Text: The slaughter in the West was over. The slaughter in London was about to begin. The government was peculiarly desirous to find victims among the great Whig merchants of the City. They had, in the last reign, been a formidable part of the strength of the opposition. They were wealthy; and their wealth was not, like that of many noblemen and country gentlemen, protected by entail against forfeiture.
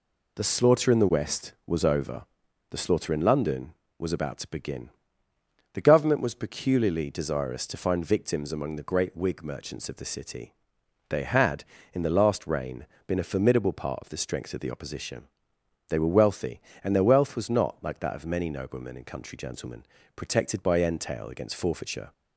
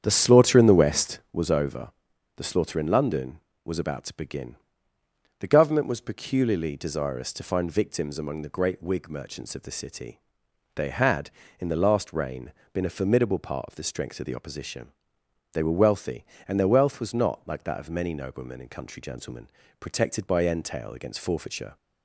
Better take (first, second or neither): first